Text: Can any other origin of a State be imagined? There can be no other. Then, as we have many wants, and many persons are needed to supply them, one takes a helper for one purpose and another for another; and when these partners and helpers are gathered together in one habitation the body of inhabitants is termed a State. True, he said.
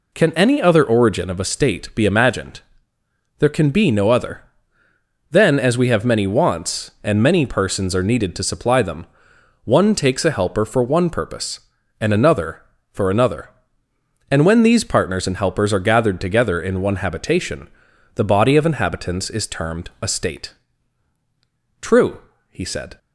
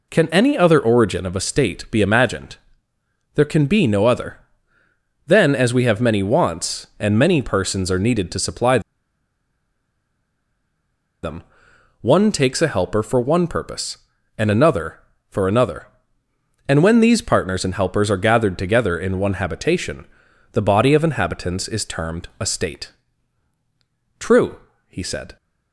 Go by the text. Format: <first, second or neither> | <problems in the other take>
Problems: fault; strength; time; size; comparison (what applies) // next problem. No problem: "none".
first | pauses between "supply" and "them"; strong; at 8.7 s; 2.4 s long // pauses between "habitation" and "the"; at 20.0 s; 0.44 s long; also in the first